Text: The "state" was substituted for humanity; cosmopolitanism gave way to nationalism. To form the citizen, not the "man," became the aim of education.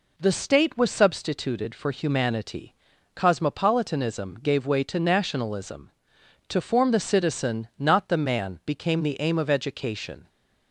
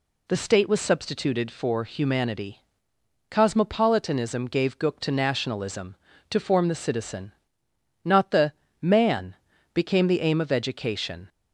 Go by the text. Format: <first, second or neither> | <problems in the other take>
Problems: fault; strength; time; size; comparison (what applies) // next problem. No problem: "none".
first | says "gook" for "way"; at 4.7 s // pauses between "the" and "man"; slight; at 8.5 s; 0.26 s long